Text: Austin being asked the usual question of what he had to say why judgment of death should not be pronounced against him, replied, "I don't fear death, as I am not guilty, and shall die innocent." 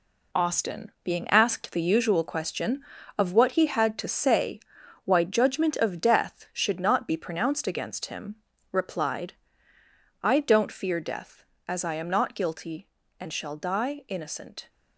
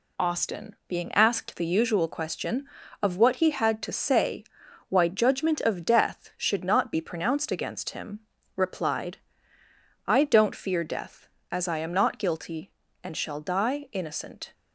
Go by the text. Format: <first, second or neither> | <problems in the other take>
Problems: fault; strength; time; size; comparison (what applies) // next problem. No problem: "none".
second | gets quieter; strong; throughout; 7.5 dB // pauses between "say" and "why"; at 4.5 s; 0.44 s long; also in the second